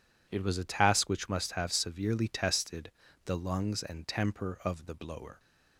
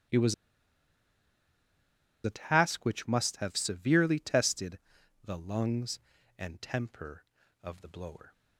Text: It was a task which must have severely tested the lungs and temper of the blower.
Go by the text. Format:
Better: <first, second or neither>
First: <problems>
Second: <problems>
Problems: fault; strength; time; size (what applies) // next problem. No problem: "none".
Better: first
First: pauses between "tested" and "the"; slight; at 2.8 s; 0.36 s long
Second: starts louder than the rest; strong; until 3.0 s; 11.5 dB // pauses between "was" and "a"; strong; at 0.3 s; 1.8 s long // pauses between "tested" and "the"; noticeable; at 4.7 s; 0.46 s long